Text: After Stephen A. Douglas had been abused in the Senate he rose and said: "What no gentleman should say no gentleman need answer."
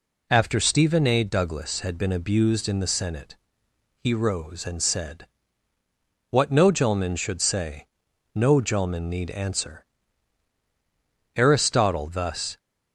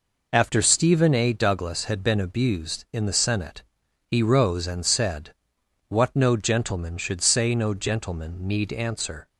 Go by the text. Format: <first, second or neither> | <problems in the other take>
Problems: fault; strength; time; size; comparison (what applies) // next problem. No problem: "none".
second | pauses between "Senate" and "he"; noticeable; at 3.3 s; 0.62 s long; also in the second // pauses between "say" and "no"; noticeable; at 7.8 s; 0.50 s long // goes on to say "Aristotle thus"; noticeable; from 11.3 s on; 1.2 s long